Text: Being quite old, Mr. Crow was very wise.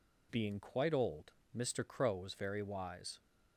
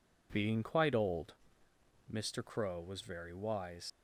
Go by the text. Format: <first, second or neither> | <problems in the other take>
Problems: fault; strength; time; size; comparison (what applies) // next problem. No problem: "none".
first | leaves "wise" unfinished; at 3.8 s; 90 ms